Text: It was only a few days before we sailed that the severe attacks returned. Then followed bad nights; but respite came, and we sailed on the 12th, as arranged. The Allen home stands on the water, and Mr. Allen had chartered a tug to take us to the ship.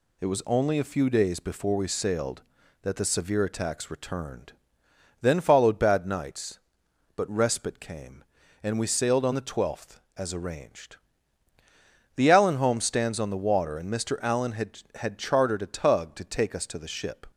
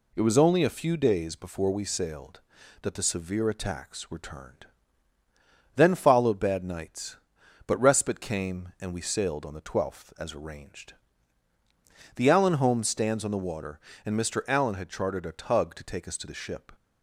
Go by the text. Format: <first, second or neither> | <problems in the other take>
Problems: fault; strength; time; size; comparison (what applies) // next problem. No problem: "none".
second | says "had" twice; at 14.9 s